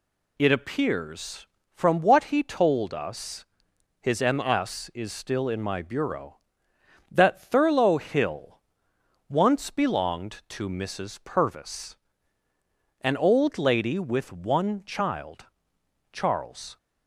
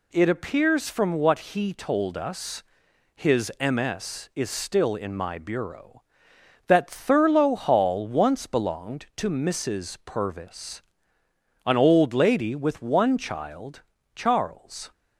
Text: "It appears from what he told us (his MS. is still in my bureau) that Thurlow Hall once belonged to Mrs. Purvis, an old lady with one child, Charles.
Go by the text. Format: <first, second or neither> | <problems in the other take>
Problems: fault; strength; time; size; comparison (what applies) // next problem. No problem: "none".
second | says "Hill" for "Hall"; at 7.9 s